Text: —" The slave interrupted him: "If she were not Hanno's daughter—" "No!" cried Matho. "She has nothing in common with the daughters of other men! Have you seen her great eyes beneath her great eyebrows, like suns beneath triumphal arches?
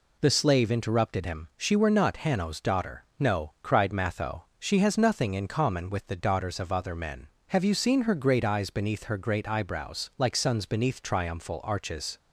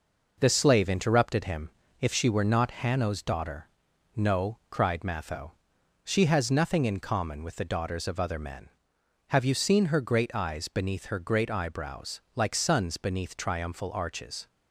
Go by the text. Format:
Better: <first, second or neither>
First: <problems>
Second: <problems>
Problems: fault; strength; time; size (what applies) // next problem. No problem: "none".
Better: second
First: skips "If"; at 1.5 s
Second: none